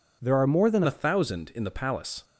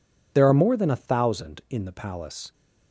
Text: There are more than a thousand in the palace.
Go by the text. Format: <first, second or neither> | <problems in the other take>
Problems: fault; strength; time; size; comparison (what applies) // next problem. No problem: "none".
second | changes voice at "a"; from 0.8 s on; 1.4 s long